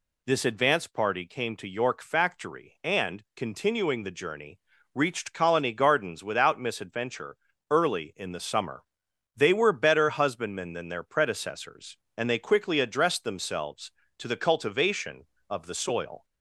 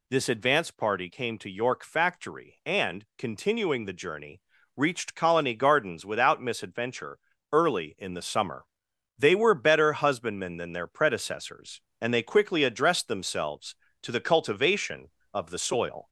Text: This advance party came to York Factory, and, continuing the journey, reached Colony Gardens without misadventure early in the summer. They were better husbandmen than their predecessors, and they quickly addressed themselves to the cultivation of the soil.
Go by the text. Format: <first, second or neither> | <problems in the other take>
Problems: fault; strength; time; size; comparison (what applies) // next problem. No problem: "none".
first | gets louder; slight; throughout; 2.5 dB // pauses between "misadventure" and "early"; slight; at 7.1 s; 0.34 s long; slight in the first